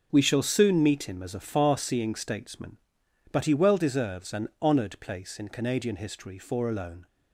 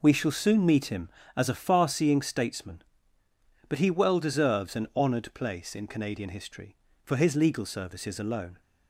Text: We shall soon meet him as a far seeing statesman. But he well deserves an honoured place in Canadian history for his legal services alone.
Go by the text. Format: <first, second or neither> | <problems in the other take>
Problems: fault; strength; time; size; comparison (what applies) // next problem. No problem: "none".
second | skips "his legal services"; at 6.6 s